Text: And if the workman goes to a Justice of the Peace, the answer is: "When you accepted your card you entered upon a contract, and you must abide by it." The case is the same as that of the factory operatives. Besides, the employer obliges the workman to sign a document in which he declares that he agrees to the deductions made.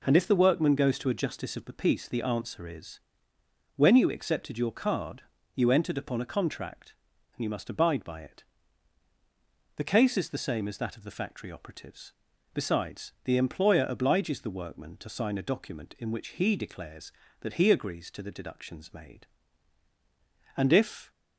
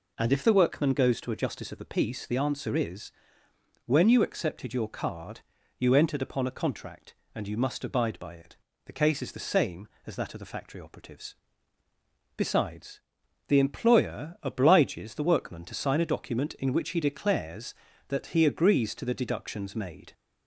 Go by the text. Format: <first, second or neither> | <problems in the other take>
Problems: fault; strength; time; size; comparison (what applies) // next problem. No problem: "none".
second | pauses between "card" and "you"; slight; at 5.2 s; 0.32 s long; slight in the second // goes on to say "And if"; from 20.5 s on; 0.54 s long